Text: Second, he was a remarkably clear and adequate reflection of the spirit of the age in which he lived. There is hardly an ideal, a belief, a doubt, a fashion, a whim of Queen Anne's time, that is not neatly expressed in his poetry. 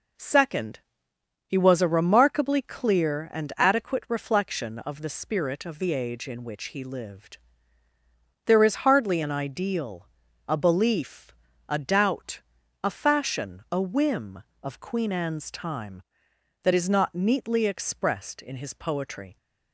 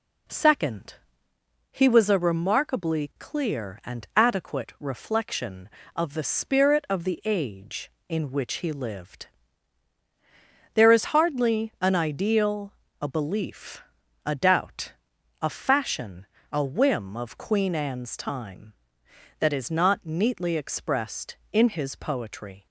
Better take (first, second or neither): neither